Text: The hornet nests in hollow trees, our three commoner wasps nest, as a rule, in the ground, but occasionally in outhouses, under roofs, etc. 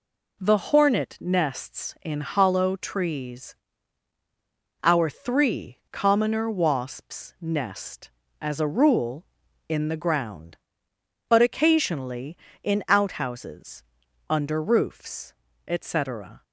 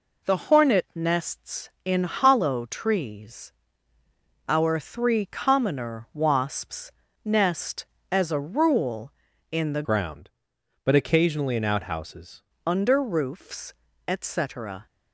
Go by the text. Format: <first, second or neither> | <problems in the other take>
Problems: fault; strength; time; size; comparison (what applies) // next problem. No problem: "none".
first | pauses between "wasps" and "nest"; slight; at 6.9 s; 0.32 s long // changes voice from "ground" to "outhouses"; from 9.8 to 12.4 s; 2.6 s long